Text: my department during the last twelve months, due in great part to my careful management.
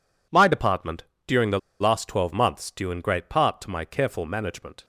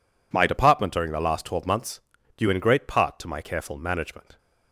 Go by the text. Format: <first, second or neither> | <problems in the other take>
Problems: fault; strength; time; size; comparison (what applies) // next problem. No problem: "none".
second | pauses between "department" and "during"; slight; at 1.0 s; 0.22 s long // pauses between "the" and "last"; slight; at 1.5 s; 0.22 s long